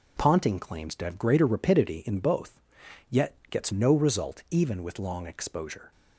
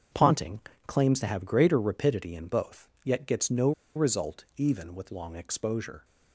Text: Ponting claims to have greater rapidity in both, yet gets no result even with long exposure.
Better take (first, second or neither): first